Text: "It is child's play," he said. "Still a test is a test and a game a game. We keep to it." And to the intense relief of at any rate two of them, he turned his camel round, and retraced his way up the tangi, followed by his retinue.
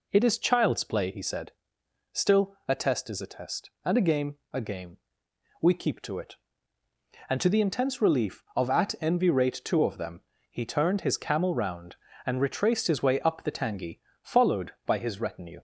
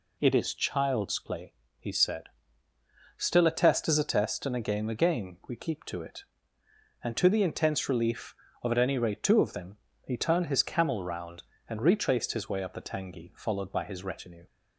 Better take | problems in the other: second | pauses between "game" and "a"; slight; at 4.3 s; 0.16 s long // says "envy" for "any"; at 9.0 s

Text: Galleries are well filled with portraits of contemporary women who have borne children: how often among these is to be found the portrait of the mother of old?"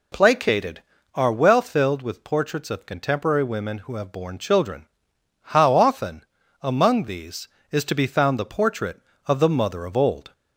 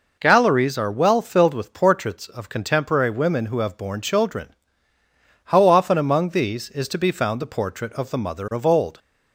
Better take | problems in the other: second | says "Placated" for "Galleries"; at 0.1 s // pauses between "often" and "among"; at 6.2 s; 0.38 s long

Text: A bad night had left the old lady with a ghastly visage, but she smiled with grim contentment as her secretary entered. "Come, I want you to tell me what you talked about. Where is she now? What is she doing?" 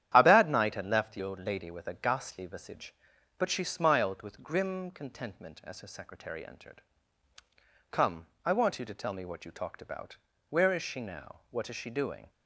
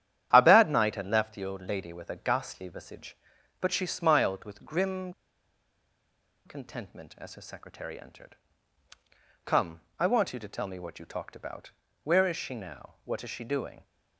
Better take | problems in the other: first | starts louder than the rest; strong; until 1.3 s; 10.5 dB; strong in the first // pauses between "grim" and "contentment"; strong; at 5.1 s; 1.3 s long

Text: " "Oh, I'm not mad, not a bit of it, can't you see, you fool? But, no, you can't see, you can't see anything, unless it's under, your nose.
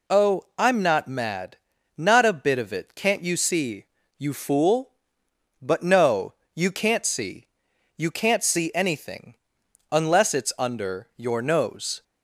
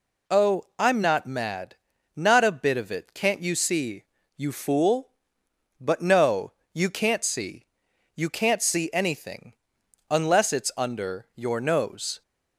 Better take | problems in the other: neither | none

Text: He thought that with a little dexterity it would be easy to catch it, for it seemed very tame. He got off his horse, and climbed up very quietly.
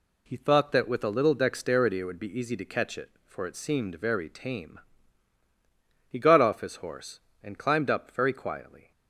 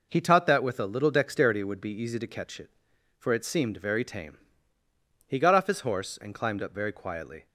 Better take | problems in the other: first | says "taught" for "thought"; at 0.1 s

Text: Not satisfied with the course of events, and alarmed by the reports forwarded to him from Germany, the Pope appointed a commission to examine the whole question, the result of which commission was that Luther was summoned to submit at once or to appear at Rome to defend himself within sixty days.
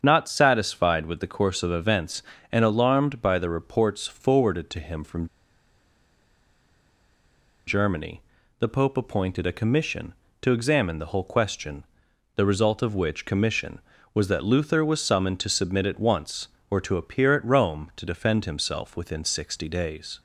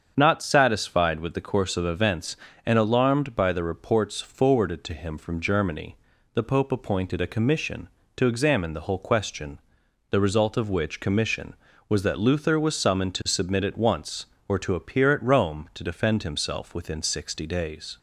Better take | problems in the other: second | starts louder than the rest; strong; until 1.0 s; 7.5 dB; strong in the second // pauses between "from" and "Germany"; strong; at 5.2 s; 2.4 s long

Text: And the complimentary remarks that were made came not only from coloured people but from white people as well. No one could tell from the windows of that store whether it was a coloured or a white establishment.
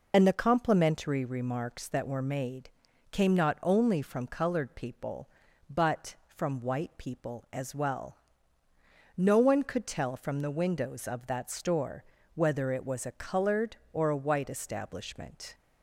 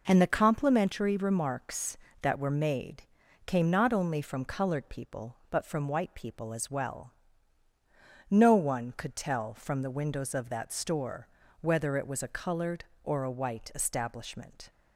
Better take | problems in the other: second | loses the start of "And"; at 0.1 s; 60 ms // pauses between "made" and "came"; at 2.6 s; 0.42 s long; also in the second // pauses between "store" and "whether"; slight; at 12.0 s; 0.30 s long; slight in the second

